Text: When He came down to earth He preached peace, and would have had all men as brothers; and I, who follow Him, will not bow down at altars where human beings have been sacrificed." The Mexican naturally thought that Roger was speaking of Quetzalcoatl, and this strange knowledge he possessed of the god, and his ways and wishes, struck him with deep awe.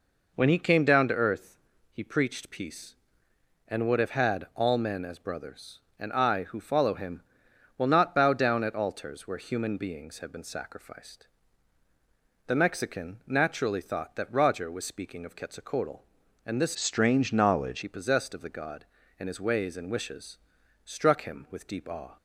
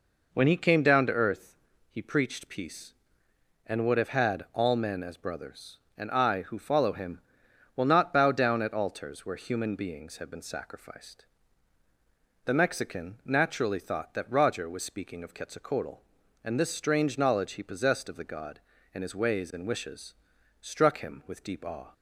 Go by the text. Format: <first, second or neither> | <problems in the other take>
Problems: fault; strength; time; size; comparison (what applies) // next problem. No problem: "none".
second | pauses between "earth" and "He"; slight; at 1.5 s; 0.34 s long; slight in the second // changes voice from "strange" to "knowledge"; from 16.7 to 17.8 s; 1.1 s long